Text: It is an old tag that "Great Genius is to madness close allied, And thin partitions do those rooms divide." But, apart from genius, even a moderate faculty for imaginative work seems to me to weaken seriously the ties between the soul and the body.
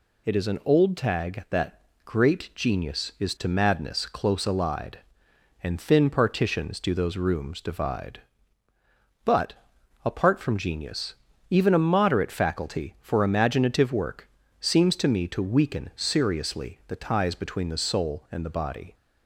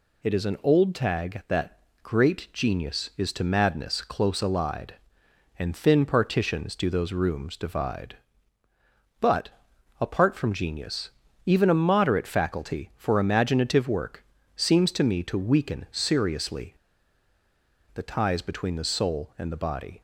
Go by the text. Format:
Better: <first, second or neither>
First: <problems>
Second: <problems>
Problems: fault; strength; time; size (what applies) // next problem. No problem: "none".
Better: first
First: pauses between "that" and "Great"; slight; at 1.8 s; 0.22 s long // pauses between "work" and "seems"; slight; at 14.2 s; 0.32 s long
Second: pauses between "that" and "Great"; slight; at 1.7 s; 0.22 s long // pauses between "work" and "seems"; slight; at 14.2 s; 0.32 s long // pauses between "seriously" and "the"; at 16.7 s; 1.1 s long